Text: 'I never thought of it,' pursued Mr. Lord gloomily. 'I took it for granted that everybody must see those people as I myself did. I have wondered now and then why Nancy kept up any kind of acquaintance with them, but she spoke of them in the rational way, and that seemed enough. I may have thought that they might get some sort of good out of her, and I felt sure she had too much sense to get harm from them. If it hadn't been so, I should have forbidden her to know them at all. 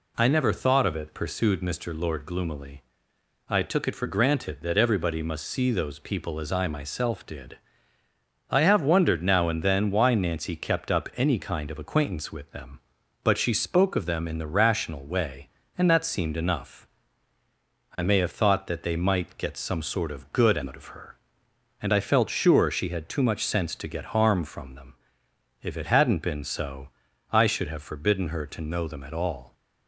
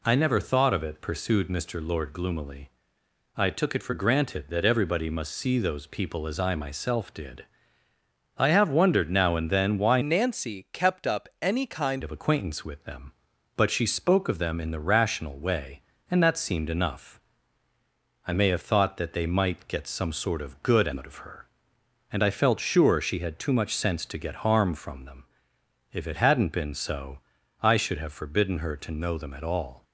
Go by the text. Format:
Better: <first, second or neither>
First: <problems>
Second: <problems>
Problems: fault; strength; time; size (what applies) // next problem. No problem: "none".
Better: first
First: none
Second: changes voice from "Nancy" to "kind"; from 10.0 to 12.0 s; 2.0 s long